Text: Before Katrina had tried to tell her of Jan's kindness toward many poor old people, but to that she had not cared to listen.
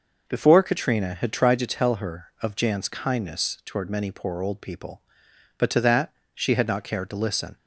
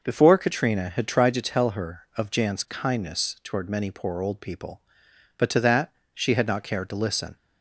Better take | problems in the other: neither | pauses between "that" and "she"; slight; the same in both

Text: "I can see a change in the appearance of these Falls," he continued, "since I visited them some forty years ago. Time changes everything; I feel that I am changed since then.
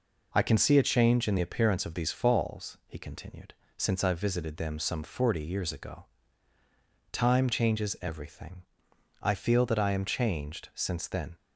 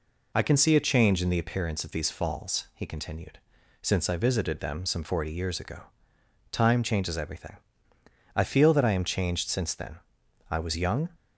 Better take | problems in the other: first | goes on to say "I was young"; noticeable; from 10.4 s on; 0.62 s long

